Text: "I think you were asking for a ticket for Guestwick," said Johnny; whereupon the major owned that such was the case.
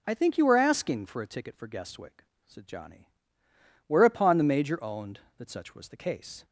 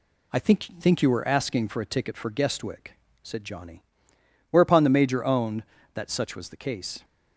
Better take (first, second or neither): first